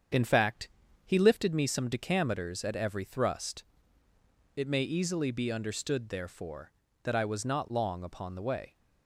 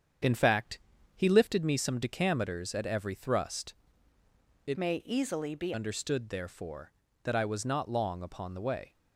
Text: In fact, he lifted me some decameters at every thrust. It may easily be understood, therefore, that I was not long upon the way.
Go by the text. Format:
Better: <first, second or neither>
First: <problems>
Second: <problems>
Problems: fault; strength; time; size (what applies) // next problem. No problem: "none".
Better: first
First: starts louder than the rest; strong; until 1.5 s; 7.5 dB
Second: starts louder than the rest; strong; until 1.6 s; 8 dB // changes voice from "may" to "be"; from 4.7 to 5.7 s; 1.0 s long